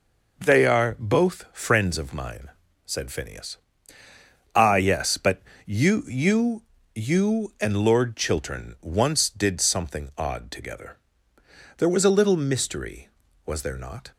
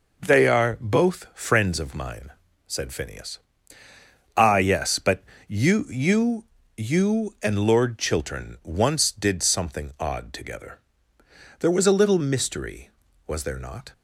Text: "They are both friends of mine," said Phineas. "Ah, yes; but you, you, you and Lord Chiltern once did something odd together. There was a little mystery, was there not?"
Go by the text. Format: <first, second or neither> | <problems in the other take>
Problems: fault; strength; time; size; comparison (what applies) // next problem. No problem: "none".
neither | pauses between "but" and "you"; slight; the same in both